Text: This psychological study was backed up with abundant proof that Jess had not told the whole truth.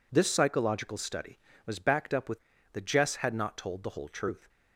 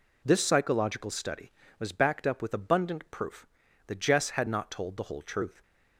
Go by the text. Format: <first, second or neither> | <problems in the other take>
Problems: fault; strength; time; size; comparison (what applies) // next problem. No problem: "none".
second | skips "abundant proof"; at 2.5 s